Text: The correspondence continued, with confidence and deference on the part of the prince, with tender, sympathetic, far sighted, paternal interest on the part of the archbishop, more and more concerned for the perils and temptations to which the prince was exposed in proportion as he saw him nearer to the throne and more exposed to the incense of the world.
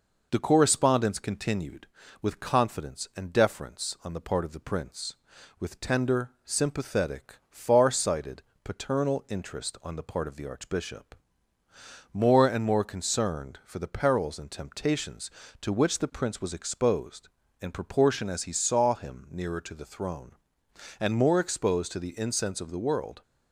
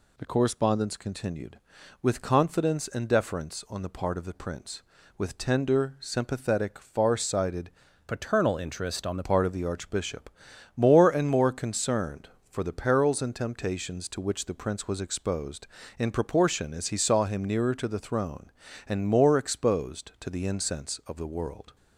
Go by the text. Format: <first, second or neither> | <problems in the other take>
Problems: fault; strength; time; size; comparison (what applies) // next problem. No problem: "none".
first | changes voice from "paternal" to "the"; from 8.0 to 9.2 s; 1.2 s long